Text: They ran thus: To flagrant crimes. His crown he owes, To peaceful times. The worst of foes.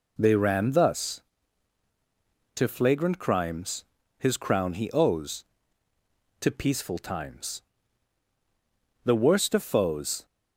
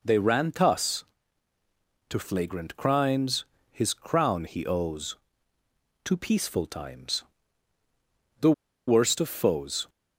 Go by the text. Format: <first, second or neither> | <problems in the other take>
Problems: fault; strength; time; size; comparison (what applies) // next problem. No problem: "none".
first | pauses between "The" and "worst"; slight; at 8.5 s; 0.35 s long